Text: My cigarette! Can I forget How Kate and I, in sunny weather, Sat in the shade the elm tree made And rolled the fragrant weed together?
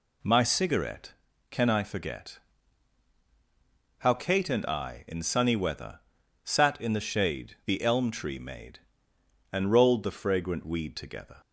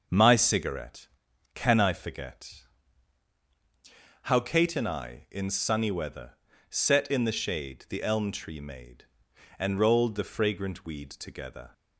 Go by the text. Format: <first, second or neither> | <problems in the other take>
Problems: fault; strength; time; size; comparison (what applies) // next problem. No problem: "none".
first | starts louder than the rest; noticeable; until 1.5 s; 6 dB // pauses between "forget" and "How"; strong; at 2.6 s; 1.6 s long; strong in the first // says "Set" for "Sat"; at 6.7 s